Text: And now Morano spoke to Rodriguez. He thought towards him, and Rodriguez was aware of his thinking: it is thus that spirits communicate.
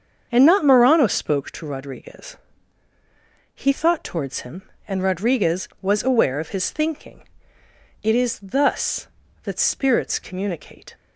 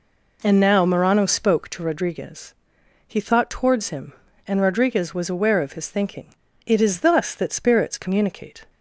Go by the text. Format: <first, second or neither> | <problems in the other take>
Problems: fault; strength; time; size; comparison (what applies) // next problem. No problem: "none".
second | starts louder than the rest; until 1.3 s; 7 dB // says "not" for "now"; at 0.4 s